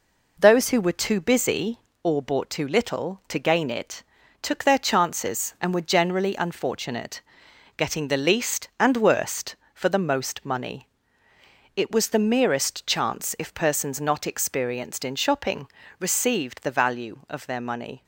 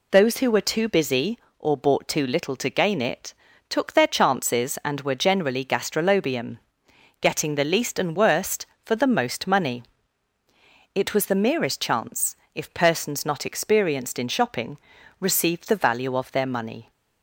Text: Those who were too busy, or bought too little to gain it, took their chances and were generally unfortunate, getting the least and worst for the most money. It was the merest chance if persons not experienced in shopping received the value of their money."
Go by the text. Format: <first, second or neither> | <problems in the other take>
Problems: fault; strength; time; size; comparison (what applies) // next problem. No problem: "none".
first | says "gastrolobium" for "unfortunate"; at 5.6 s // pauses between "chance" and "if"; slight; at 12.3 s; 0.18 s long // pauses between "shopping" and "received"; at 14.7 s; 0.42 s long; slight in the first